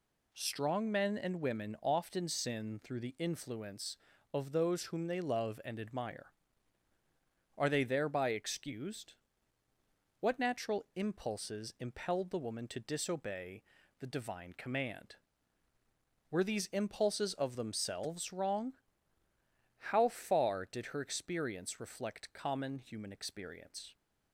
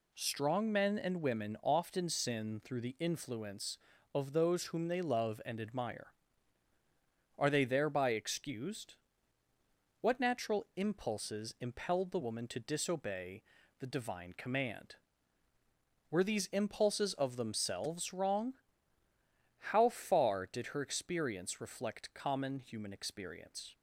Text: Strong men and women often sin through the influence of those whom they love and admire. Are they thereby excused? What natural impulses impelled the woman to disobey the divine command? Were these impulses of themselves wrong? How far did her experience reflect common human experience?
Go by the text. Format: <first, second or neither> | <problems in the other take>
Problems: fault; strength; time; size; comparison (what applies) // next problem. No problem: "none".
neither | pauses between "disobey" and "the"; the same in both